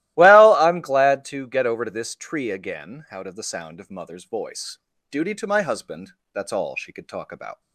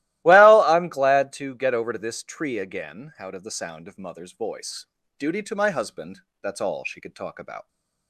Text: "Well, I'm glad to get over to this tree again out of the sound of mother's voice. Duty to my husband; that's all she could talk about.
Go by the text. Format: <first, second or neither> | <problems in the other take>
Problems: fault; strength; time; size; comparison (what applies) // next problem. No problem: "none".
neither | starts louder than the rest; strong; the same in both